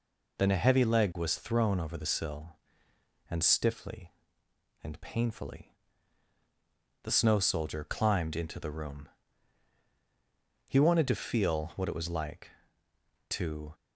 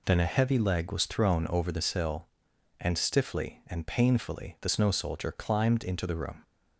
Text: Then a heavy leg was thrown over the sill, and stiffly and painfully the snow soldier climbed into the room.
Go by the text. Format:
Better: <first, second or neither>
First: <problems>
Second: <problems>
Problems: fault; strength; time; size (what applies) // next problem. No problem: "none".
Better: second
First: pauses between "painfully" and "the"; strong; at 5.7 s; 1.3 s long // goes on to say "He wanted to feel what it was like to"; strong; from 10.6 s on; 3.0 s long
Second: none